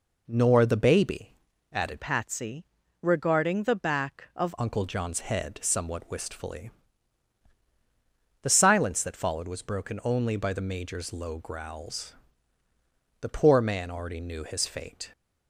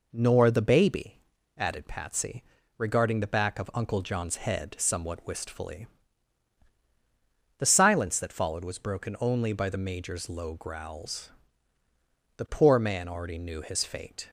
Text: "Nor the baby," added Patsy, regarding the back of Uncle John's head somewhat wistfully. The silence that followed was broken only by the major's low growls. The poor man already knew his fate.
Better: second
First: changes voice from "Patsy" to "of"; from 2.0 to 4.5 s; 2.5 s long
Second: none

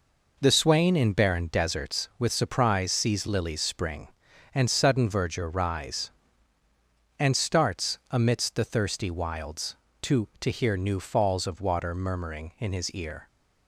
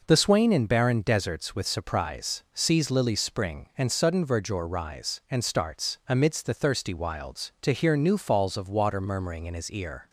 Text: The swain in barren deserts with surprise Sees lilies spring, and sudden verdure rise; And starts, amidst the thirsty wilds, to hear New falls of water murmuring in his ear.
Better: second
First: says "to" twice; at 10.4 s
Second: none

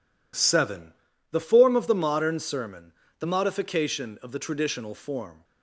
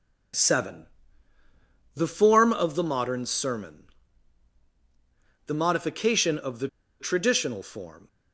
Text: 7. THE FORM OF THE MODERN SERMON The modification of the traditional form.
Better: first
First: pauses between "SERMON" and "The"; slight; at 2.9 s; 0.26 s long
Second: pauses between "SERMON" and "The"; strong; at 3.8 s; 1.6 s long // pauses between "the" and "traditional"; slight; at 6.6 s; 0.33 s long

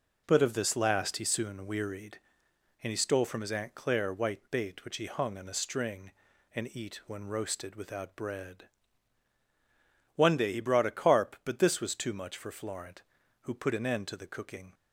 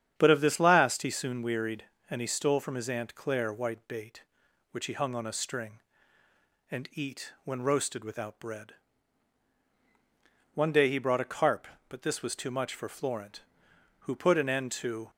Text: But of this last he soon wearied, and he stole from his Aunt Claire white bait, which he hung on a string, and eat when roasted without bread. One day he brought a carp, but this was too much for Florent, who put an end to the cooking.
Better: first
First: none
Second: starts louder than the rest; strong; until 1.1 s; 9 dB // stops before "the cooking"; at 15.0 s

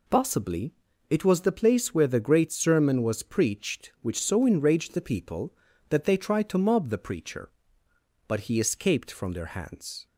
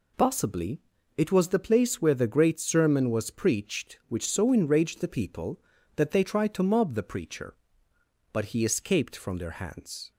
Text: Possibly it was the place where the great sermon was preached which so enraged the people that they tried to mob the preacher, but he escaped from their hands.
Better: neither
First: pauses between "Possibly" and "it"; at 0.7 s; 0.38 s long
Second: pauses between "Possibly" and "it"; at 0.7 s; 0.38 s long

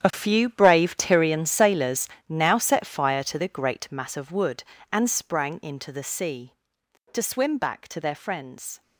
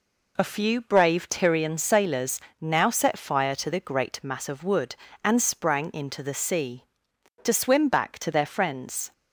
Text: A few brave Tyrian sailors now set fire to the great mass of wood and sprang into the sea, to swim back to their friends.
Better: second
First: gets quieter; strong; throughout; 14.5 dB // pauses between "sailors" and "now"; slight; at 2.0 s; 0.18 s long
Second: pauses between "sailors" and "now"; slight; at 2.4 s; 0.18 s long

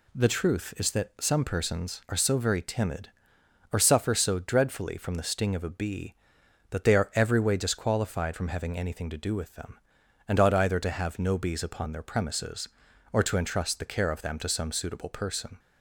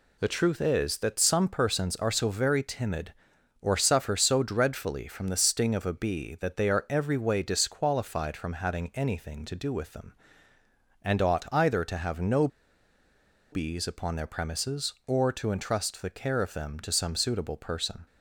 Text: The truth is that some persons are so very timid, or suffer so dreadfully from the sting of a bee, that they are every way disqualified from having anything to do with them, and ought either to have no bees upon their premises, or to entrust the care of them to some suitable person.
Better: first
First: none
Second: pauses between "no" and "bees"; at 12.4 s; 1.0 s long

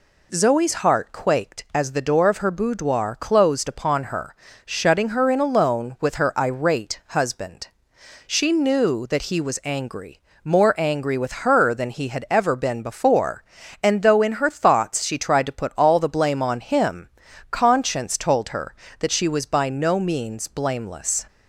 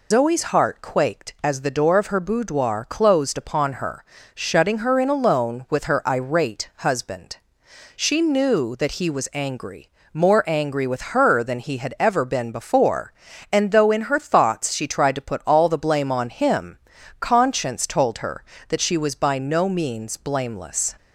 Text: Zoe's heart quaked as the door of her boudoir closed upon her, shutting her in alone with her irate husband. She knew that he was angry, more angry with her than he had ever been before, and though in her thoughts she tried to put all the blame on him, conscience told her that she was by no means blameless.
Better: first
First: none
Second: loses the start of "Zoe's"; at 0.1 s; 100 ms

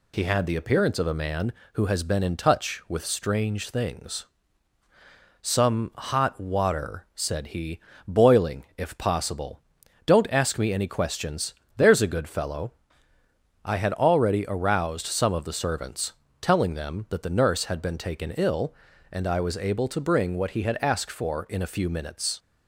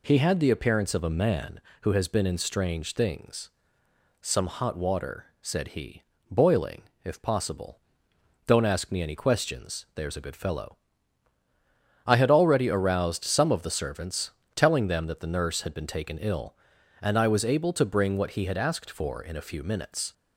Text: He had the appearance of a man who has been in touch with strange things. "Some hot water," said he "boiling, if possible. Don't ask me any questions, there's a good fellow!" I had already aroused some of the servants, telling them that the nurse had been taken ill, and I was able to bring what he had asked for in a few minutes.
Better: first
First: pauses between "he" and "boiling"; slight; at 7.8 s; 0.26 s long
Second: skips "touch with"; at 2.3 s // pauses between "he" and "boiling"; slight; at 6.0 s; 0.26 s long

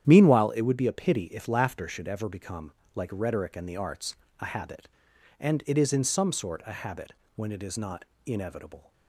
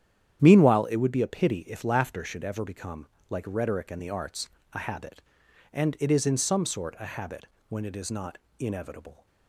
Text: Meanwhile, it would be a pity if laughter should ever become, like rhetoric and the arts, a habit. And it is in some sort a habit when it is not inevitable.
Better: neither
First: starts louder than the rest; strong; until 1.0 s; 9.5 dB // pauses between "habit" and "when"; slight; at 7.1 s; 0.24 s long // pauses between "not" and "inevitable"; slight; at 8.0 s; 0.22 s long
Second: starts louder than the rest; strong; until 1.4 s; 9.5 dB // pauses between "habit" and "when"; slight; at 7.4 s; 0.24 s long // pauses between "not" and "inevitable"; slight; at 8.3 s; 0.22 s long

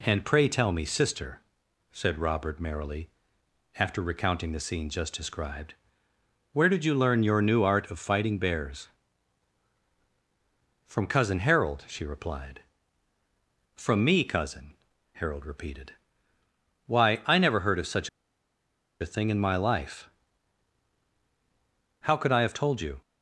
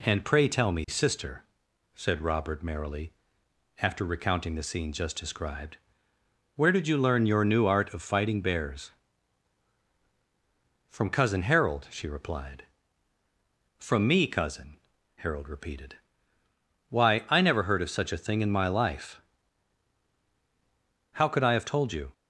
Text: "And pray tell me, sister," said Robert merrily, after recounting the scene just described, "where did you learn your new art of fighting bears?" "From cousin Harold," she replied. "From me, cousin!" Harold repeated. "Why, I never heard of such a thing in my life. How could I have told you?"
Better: second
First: pauses between "such" and "a"; noticeable; at 18.0 s; 0.91 s long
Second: none

